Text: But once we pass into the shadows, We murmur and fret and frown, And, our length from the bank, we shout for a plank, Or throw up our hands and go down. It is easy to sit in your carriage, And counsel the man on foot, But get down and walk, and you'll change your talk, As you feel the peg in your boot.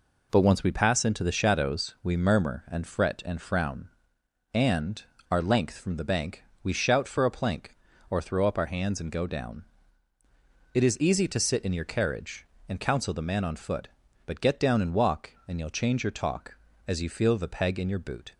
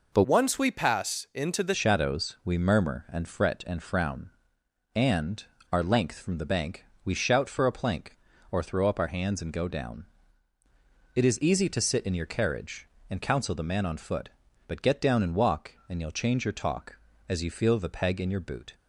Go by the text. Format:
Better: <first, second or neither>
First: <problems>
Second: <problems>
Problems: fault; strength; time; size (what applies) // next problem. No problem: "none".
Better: first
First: none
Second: changes voice from "once" to "the"; from 0.2 to 1.7 s; 1.5 s long